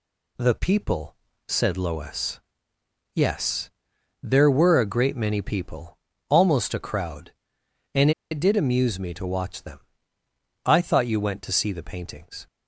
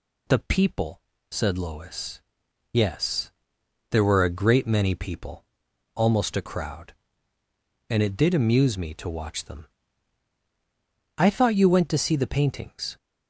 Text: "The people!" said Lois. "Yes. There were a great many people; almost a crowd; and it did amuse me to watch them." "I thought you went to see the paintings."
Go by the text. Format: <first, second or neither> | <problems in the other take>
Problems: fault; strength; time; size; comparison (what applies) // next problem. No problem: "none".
second | pauses between "and" and "it"; slight; at 8.1 s; 0.20 s long